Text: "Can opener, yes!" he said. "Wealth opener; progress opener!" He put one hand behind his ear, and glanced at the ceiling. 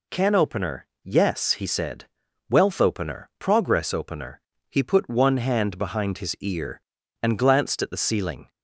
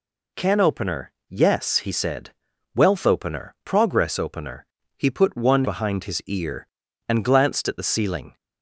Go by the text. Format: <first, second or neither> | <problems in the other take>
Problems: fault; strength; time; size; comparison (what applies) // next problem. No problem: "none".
first | skips "hand"; at 5.6 s